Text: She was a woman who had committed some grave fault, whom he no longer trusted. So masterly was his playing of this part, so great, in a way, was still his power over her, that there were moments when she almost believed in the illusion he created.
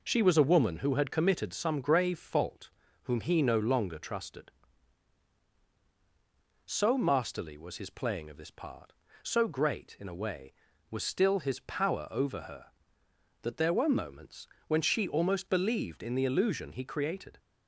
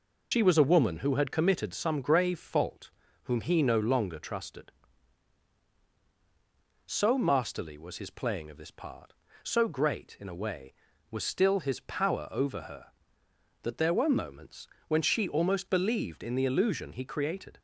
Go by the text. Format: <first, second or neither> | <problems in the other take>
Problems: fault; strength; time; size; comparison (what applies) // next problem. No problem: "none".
first | loses the start of "She"; at 0.3 s; 90 ms // pauses between "moments" and "when"; slight; at 14.6 s; 0.22 s long; slight in the first